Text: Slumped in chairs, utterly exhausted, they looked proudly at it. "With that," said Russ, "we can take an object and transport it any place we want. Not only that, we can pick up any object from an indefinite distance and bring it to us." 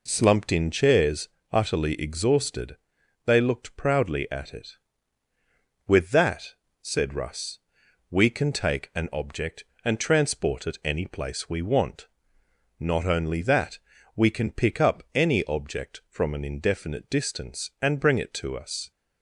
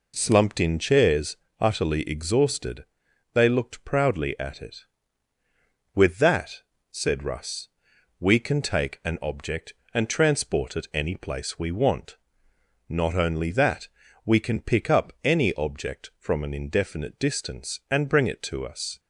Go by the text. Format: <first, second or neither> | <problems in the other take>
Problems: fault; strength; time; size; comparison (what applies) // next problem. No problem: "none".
neither | none